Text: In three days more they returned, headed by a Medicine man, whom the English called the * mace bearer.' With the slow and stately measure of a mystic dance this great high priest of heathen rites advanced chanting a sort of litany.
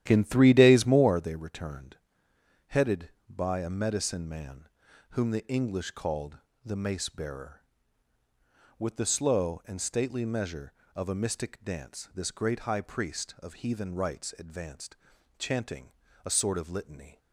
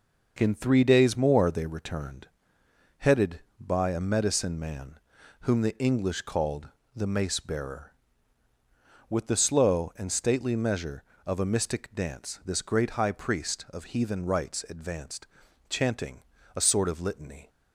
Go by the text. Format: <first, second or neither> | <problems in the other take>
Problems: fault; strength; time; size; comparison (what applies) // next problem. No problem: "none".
second | starts louder than the rest; strong; until 1.1 s; 11.5 dB // pauses between "called" and "the"; slight; at 6.3 s; 0.26 s long; slight in the second // pauses between "advanced" and "chanting"; at 14.9 s; 0.44 s long; also in the second // pauses between "chanting" and "a"; slight; at 15.9 s; 0.34 s long; slight in the second